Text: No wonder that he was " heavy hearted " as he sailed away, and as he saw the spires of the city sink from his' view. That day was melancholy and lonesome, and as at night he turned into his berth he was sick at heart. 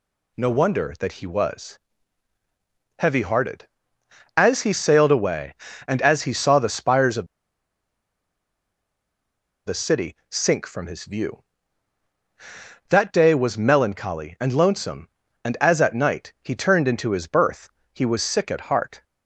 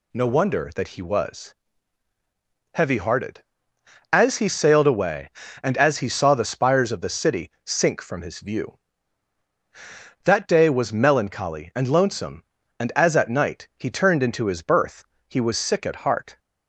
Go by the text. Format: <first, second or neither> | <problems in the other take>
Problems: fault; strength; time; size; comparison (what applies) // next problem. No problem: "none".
second | pauses between "of" and "the"; strong; at 7.2 s; 2.4 s long // pauses between "city" and "sink"; slight; at 10.1 s; 0.16 s long; slight in the second // pauses between "berth" and "he"; slight; at 17.6 s; 0.24 s long; slight in the second